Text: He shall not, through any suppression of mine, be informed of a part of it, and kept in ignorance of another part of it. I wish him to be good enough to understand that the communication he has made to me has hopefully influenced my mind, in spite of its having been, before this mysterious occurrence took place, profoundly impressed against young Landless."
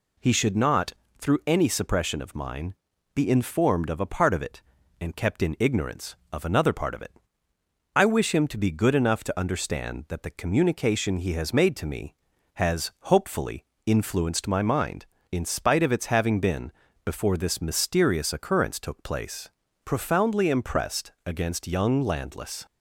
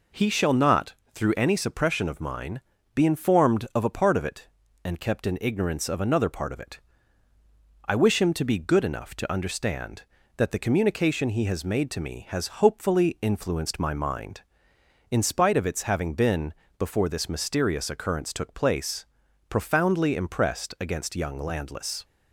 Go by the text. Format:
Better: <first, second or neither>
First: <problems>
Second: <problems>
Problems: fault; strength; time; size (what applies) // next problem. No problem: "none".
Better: second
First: says "should" for "shall"; at 0.3 s // pauses between "hopefully" and "influenced"; slight; at 13.6 s; 0.22 s long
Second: none